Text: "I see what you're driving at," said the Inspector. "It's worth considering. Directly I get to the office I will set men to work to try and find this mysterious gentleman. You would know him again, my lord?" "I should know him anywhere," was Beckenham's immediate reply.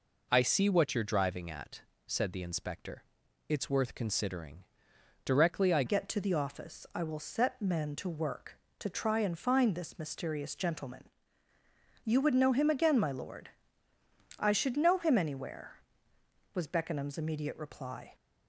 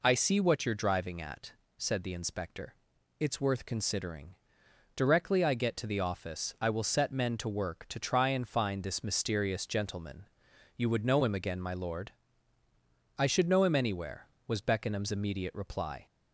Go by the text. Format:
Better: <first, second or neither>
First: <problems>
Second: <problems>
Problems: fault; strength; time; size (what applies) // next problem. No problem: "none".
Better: second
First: changes voice at "get"; from 5.8 s on; 12.3 s long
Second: none